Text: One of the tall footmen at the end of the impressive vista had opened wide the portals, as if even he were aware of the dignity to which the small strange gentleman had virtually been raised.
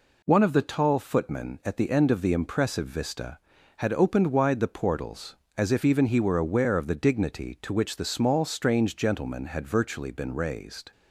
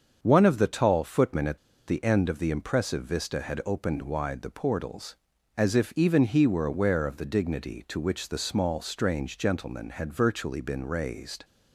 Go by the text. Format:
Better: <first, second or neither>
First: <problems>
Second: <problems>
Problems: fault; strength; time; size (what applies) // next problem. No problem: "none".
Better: first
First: none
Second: starts louder than the rest; until 1.2 s; 7 dB // pauses between "at" and "the"; slight; at 1.5 s; 0.29 s long